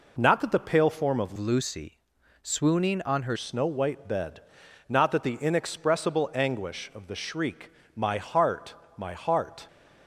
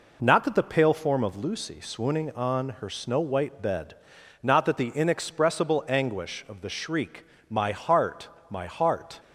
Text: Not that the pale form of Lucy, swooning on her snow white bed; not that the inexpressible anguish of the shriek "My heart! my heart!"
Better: second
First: changes voice from "Lucy" to "her"; from 1.3 to 3.3 s; 2.0 s long // pauses between "shriek" and "My"; slight; at 7.7 s; 0.24 s long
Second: pauses between "shriek" and "My"; slight; at 7.2 s; 0.24 s long

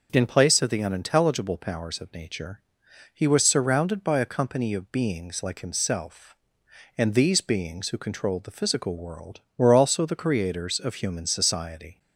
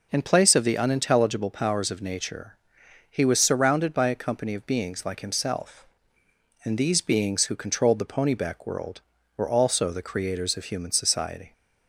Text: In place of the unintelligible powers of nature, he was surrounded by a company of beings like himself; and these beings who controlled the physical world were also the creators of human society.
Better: first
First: none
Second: says "ponyback" for "physical"; at 8.0 s

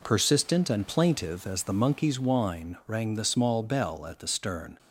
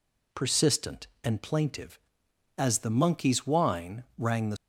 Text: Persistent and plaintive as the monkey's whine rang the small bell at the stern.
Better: first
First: none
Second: stops before "small bell at the stern"; at 4.5 s

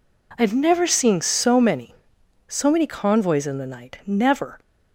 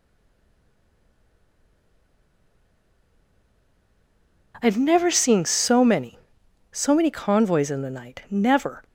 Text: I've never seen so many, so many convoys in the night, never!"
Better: first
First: none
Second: stays silent before the first word; strong; until 4.5 s; 4.5 s long

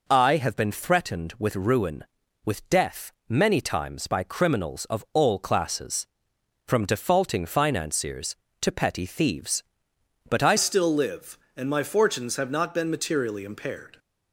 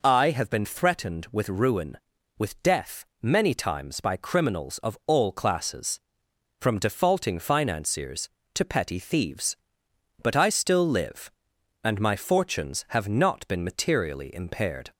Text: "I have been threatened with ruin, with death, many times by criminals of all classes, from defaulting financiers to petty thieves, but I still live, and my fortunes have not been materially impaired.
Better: second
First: changes voice at "still"; from 10.5 s on; 3.4 s long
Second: none

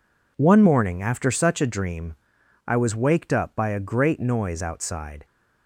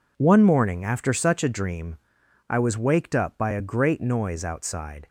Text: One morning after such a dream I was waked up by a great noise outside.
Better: neither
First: pauses between "dream" and "I"; noticeable; at 2.1 s; 0.52 s long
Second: pauses between "dream" and "I"; noticeable; at 1.9 s; 0.52 s long

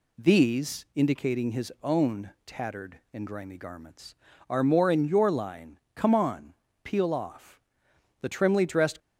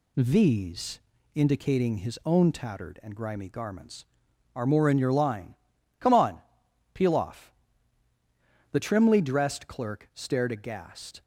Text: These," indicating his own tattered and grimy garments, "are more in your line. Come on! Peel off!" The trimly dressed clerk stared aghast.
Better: second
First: pauses between "own" and "tattered"; slight; at 2.3 s; 0.16 s long // stops before "clerk stared aghast"; at 9.0 s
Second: none

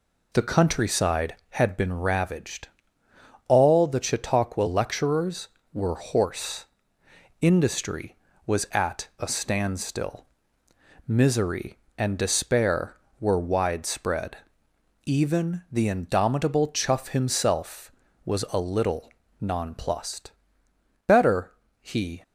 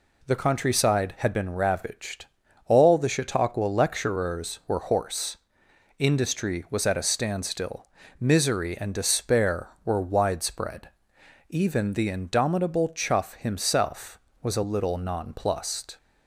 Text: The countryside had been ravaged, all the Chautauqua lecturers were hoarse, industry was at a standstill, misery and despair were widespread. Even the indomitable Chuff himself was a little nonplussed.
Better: second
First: pauses between "little" and "nonplussed"; slight; at 19.1 s; 0.30 s long // goes on to say "Better he"; noticeable; from 21.0 s on; 1.1 s long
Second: none

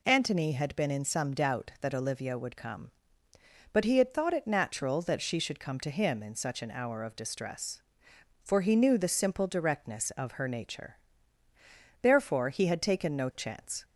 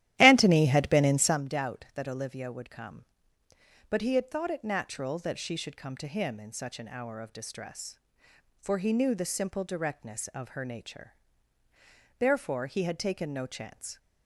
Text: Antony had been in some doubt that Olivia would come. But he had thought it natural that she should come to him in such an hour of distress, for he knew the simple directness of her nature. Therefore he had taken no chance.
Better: first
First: none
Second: starts louder than the rest; strong; until 1.4 s; 13.5 dB

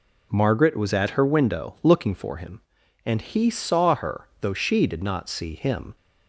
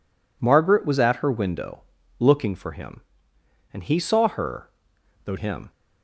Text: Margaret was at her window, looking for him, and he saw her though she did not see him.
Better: first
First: none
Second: pauses between "her" and "though"; noticeable; at 4.6 s; 0.54 s long // skips "she did not see"; at 5.3 s

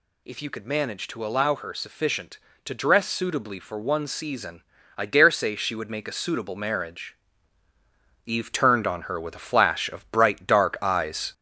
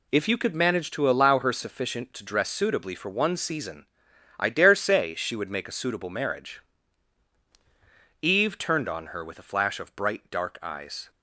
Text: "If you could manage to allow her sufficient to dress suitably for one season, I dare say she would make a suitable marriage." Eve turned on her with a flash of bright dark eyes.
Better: second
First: gets louder; slight; throughout; 3 dB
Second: none

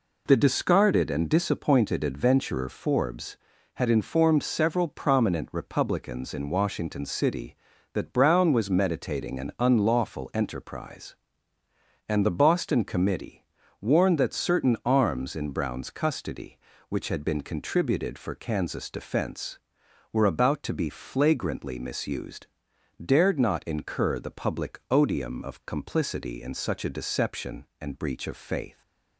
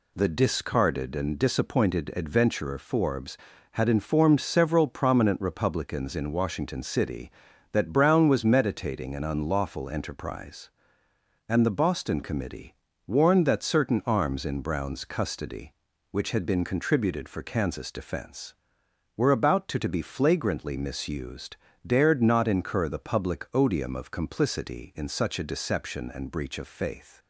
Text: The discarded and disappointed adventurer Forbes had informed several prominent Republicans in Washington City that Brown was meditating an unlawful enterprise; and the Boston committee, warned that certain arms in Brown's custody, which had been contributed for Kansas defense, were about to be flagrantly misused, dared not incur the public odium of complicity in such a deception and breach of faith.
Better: first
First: none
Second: says "to" twice; at 19.7 s

